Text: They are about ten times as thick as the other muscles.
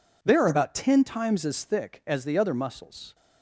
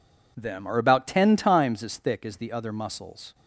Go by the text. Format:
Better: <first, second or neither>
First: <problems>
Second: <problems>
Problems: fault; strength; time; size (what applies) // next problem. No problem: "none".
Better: first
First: none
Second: says "Them" for "They"; at 0.3 s